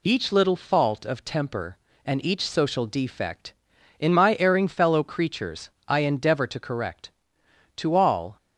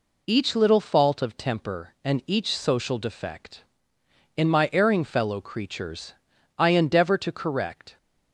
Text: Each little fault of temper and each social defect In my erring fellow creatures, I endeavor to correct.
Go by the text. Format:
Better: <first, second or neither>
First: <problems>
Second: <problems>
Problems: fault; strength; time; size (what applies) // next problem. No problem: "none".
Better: second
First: goes on to say "To all"; from 7.7 s on; 0.60 s long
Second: none